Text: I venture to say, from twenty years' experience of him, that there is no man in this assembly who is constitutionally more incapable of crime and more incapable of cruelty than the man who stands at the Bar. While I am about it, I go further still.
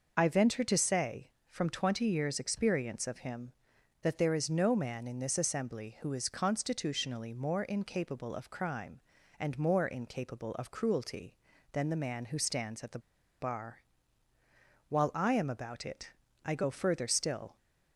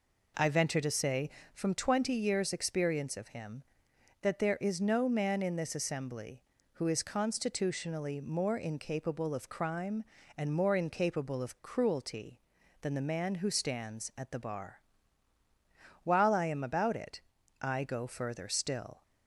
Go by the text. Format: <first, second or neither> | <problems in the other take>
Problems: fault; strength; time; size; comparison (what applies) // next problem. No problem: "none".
second | pauses between "the" and "Bar"; at 12.9 s; 0.41 s long